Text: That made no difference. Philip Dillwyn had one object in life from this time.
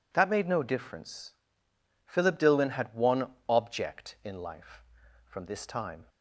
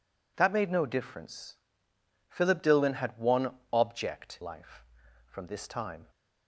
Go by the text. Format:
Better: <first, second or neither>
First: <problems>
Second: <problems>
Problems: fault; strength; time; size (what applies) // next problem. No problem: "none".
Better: first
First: pauses between "one" and "object"; slight; at 3.3 s; 0.18 s long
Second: pauses between "one" and "object"; slight; at 3.5 s; 0.18 s long // skips "in"; at 4.4 s